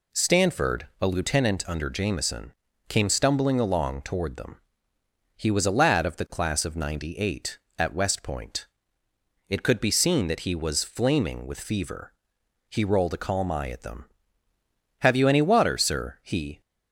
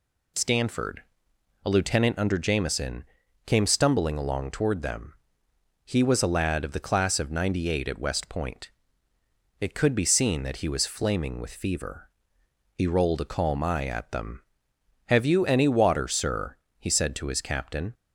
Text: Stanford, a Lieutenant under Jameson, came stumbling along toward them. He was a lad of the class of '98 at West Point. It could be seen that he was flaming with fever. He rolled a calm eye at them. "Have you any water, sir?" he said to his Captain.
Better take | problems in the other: second | stops before "said to his Captain"; at 16.6 s

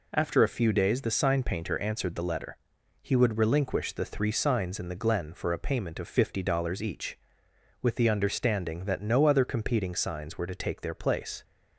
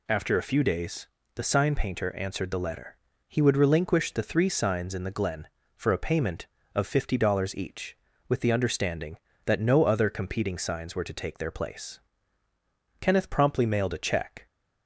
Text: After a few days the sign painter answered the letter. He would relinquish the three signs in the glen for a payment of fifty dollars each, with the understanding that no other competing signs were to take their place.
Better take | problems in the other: first | pauses between "days" and "the"; slight; at 1.0 s; 0.28 s long // goes on to say "Kenneth promptly mailed a check"; from 12.9 s on; 1.4 s long

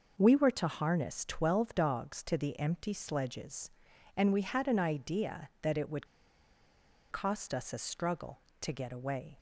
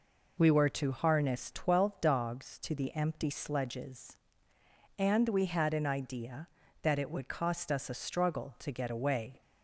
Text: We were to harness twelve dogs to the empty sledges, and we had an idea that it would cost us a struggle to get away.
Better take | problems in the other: second | pauses between "would" and "cost"; at 6.0 s; 1.0 s long

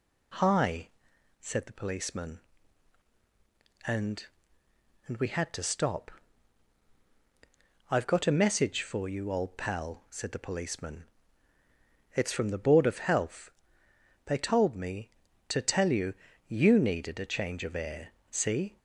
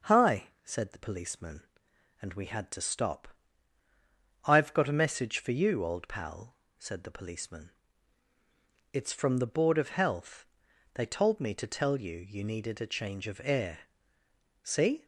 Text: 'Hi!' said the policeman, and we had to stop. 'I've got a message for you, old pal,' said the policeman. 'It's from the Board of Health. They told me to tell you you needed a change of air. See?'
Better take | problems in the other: second | says "and" twice; at 5.0 s // pauses between "you" and "you"; slight; at 16.1 s; 0.34 s long

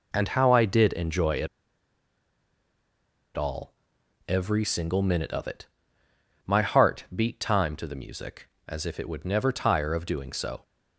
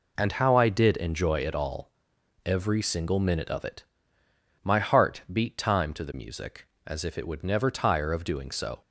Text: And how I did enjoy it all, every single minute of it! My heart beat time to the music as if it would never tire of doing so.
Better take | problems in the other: second | pauses between "it" and "all"; strong; at 1.4 s; 1.8 s long

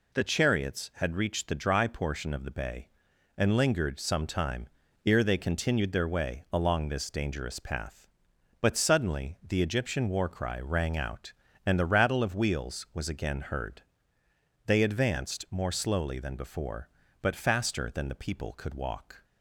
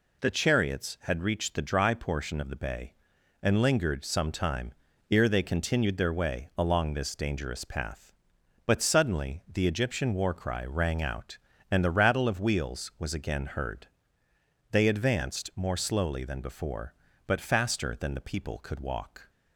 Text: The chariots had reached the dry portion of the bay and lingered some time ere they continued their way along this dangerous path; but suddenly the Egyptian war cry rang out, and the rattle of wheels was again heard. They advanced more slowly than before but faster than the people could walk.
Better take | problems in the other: neither | pauses between "time" and "ere"; the same in both

